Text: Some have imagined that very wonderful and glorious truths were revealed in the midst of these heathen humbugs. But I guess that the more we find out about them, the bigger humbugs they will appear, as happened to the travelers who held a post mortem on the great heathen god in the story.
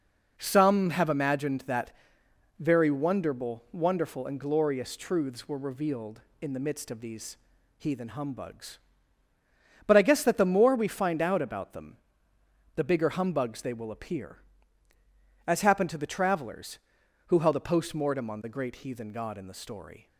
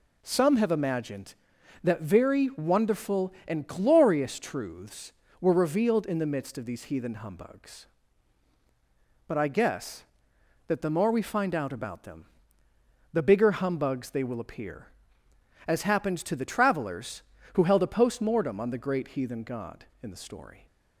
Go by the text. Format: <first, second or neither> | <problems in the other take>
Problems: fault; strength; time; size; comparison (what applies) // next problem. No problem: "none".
second | pauses between "that" and "very"; noticeable; at 1.9 s; 0.68 s long // says "wonderful" twice; at 3.7 s // pauses between "these" and "heathen"; at 7.3 s; 0.40 s long